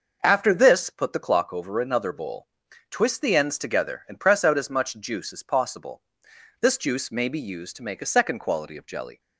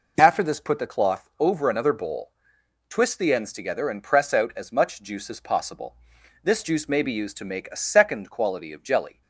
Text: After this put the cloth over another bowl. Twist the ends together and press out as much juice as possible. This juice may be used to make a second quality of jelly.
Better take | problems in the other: second | says "clock" for "cloth"; at 1.1 s

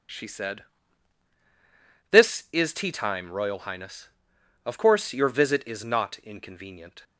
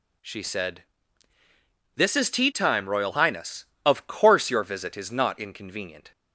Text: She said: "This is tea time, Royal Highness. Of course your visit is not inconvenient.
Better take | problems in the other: neither | none

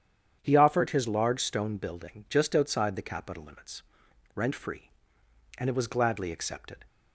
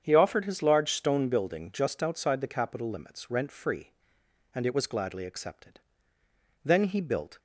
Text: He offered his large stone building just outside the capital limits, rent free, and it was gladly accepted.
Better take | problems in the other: first | starts louder than the rest; strong; until 1.0 s; 8 dB; strong in the first // goes on to say "Then he built"; noticeable; from 6.6 s on; 0.76 s long

